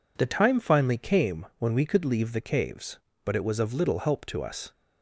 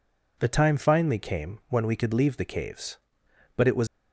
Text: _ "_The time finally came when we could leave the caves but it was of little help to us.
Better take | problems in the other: first | stops before "of little help to us"; at 3.8 s

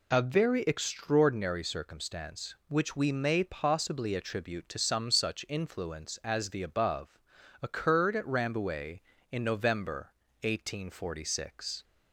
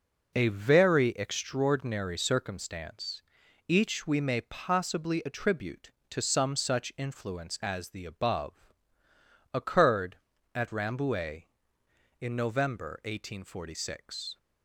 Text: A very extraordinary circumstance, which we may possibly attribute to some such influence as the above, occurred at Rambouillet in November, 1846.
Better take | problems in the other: first | says "each" for "which"; at 3.6 s

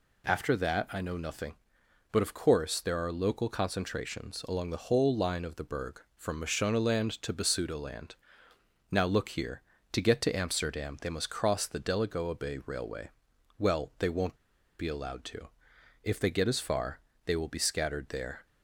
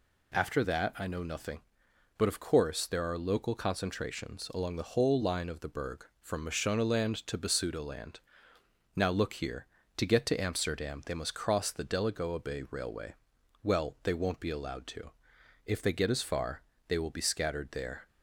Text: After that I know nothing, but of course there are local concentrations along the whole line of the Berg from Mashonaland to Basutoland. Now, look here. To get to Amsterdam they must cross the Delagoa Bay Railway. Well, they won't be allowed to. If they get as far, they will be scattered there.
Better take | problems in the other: second | pauses between "won't" and "be"; at 14.3 s; 0.43 s long

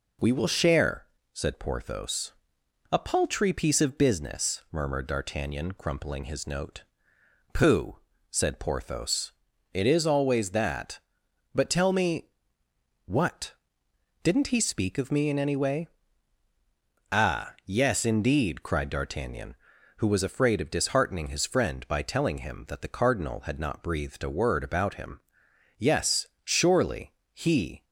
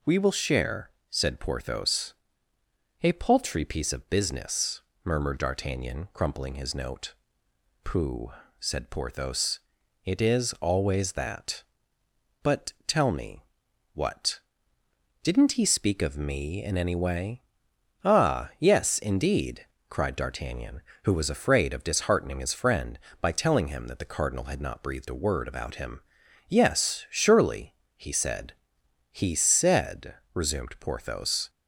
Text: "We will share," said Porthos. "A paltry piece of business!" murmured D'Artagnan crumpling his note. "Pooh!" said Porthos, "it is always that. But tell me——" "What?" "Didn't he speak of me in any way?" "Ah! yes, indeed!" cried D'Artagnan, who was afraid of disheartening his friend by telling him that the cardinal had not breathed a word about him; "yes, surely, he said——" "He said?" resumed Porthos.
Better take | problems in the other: second | stops before "said He said resumed Porthos"; at 27.8 s

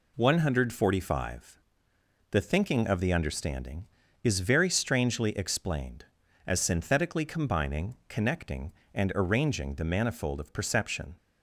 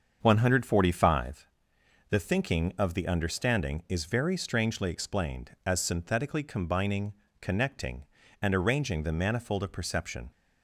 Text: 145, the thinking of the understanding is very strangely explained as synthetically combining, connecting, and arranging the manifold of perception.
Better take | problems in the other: first | starts louder than the rest; until 1.4 s; 7 dB

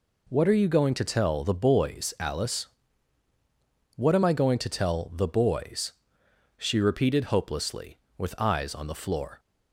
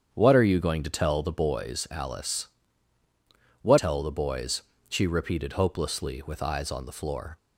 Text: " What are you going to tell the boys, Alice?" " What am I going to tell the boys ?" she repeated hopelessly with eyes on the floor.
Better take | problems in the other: first | skips "am I going to"; at 3.7 s

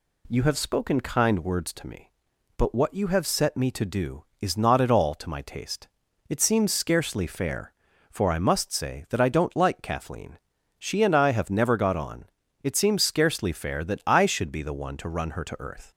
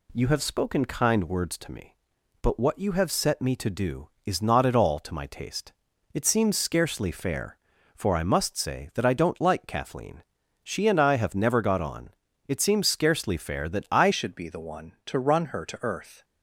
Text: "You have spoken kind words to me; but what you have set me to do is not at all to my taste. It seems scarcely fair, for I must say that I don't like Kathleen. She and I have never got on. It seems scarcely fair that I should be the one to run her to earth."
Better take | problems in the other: first | changes voice at "should"; from 14.1 s on; 2.1 s long

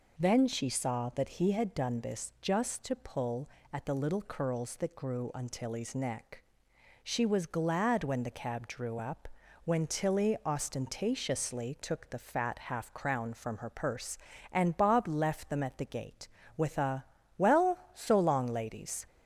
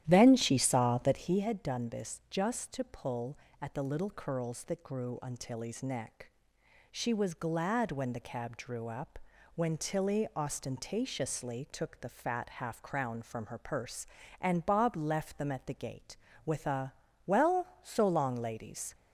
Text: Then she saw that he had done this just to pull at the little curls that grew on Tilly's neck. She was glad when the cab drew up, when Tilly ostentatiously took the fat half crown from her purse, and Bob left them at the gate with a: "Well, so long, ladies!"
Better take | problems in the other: first | starts louder than the rest; strong; until 1.4 s; 12 dB

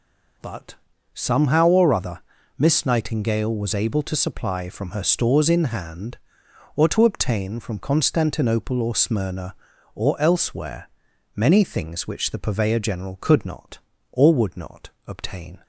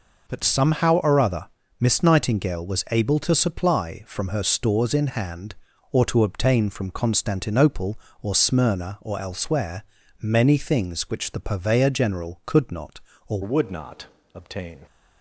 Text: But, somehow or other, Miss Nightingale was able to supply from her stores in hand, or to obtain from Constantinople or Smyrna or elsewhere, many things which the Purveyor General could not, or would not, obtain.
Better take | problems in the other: first | changes voice at "would"; from 13.4 s on; 1.3 s long

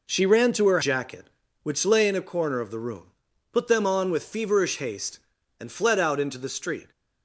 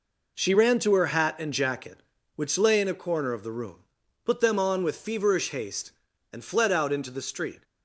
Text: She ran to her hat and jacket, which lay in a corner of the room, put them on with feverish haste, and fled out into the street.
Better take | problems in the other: second | skips "hat and"; at 0.7 s

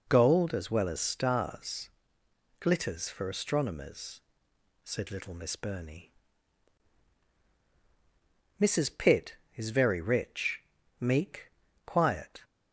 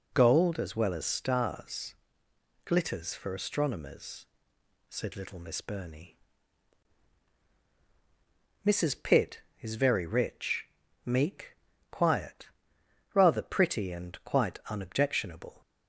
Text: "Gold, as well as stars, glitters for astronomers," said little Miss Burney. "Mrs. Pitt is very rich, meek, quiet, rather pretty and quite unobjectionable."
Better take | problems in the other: second | stops before "rather pretty and quite unobjectionable"; at 12.4 s

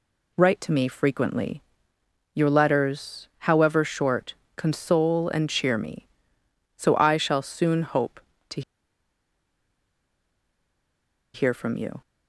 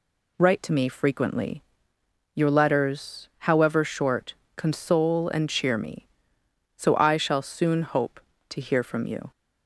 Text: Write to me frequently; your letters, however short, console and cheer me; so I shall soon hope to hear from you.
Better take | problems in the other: second | pauses between "to" and "hear"; strong; at 8.6 s; 2.7 s long

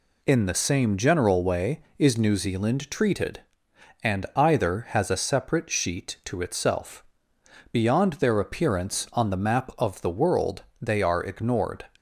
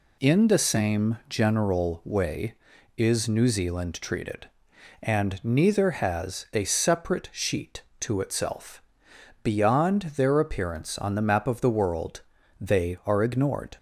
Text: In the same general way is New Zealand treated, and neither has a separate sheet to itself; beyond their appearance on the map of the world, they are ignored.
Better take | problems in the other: second | says "either" for "neither"; at 4.3 s

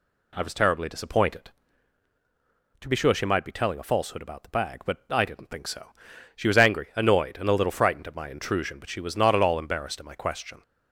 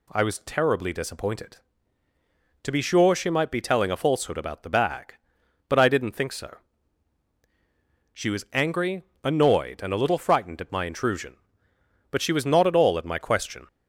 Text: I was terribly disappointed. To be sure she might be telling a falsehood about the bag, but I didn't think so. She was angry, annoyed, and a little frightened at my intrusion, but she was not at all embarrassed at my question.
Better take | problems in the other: first | skips "embarrassed"; at 12.9 s

